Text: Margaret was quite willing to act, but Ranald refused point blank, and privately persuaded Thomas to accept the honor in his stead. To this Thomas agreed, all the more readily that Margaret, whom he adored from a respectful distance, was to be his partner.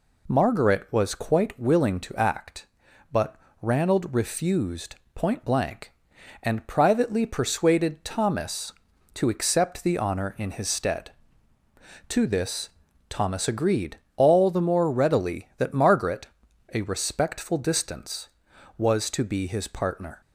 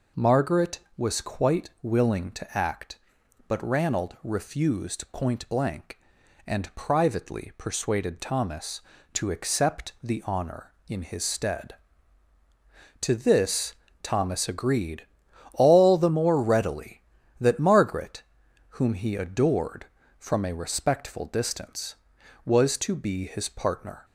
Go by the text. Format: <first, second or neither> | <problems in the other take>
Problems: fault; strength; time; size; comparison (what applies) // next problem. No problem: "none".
second | pauses between "but" and "Ranald"; slight; at 3.3 s; 0.26 s long // pauses between "refused" and "point"; slight; at 4.9 s; 0.18 s long // pauses between "this" and "Thomas"; at 12.6 s; 0.40 s long; slight in the second // skips "whom he adored from"; at 16.5 s